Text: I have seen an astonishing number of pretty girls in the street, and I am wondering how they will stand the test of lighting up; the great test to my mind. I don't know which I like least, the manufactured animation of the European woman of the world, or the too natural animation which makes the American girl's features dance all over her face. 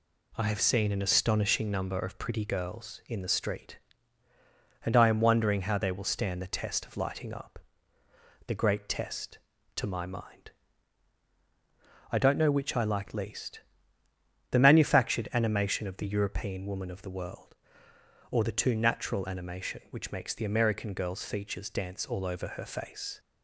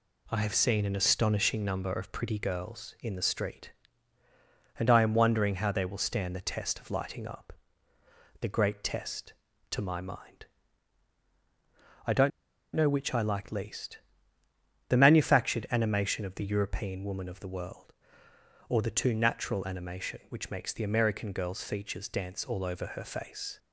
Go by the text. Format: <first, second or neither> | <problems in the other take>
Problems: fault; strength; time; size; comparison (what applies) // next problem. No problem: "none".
first | pauses between "don't" and "know"; noticeable; at 12.3 s; 0.45 s long